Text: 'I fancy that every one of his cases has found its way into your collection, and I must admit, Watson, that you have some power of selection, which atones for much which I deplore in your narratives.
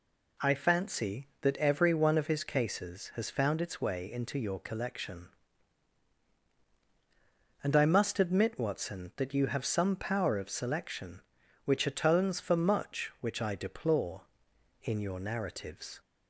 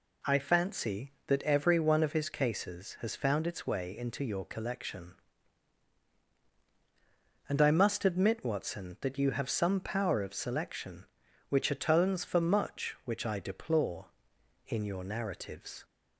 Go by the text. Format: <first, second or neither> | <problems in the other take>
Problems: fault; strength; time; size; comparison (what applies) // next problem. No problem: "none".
neither | none